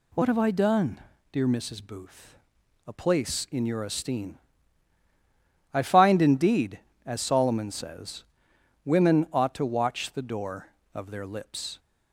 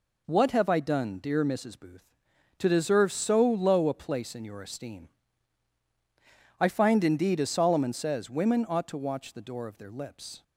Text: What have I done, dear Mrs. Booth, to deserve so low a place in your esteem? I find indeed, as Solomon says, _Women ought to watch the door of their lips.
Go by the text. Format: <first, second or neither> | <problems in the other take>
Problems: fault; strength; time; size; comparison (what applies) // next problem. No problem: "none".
second | skips "to deserve so low"; at 2.6 s